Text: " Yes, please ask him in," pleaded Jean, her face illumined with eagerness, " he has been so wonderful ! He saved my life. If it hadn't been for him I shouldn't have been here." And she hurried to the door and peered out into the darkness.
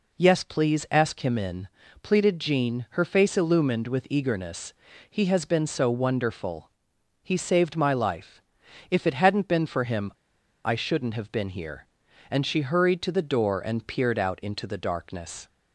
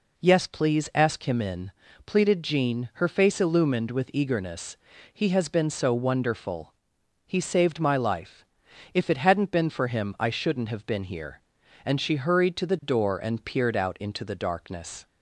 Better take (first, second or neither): second